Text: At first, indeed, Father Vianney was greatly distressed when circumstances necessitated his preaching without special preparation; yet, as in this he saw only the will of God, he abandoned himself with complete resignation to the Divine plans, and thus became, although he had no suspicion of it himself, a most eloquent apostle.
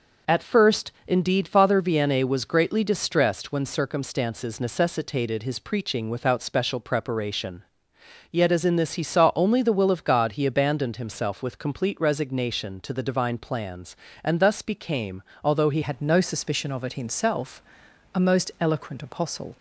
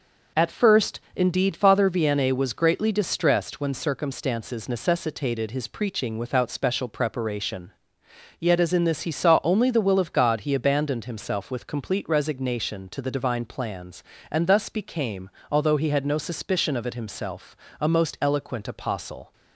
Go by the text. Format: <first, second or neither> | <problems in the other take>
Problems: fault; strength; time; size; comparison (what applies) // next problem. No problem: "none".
second | changes voice at "had"; from 15.8 s on; 3.7 s long